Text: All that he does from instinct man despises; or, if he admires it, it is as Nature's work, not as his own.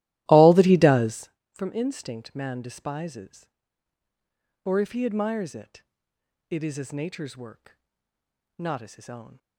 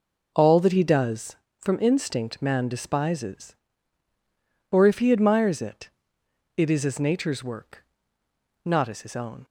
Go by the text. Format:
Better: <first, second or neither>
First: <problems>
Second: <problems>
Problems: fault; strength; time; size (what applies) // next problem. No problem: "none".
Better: second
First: starts louder than the rest; strong; until 1.3 s; 15.5 dB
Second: none